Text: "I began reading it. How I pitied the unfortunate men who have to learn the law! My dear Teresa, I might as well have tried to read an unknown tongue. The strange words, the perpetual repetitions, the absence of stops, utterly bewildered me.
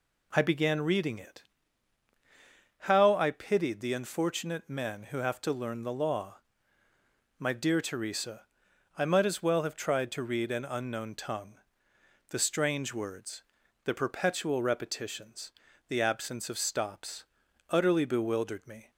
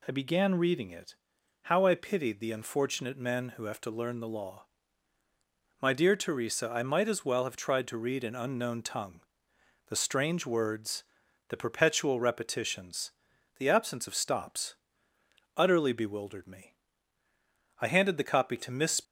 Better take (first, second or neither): first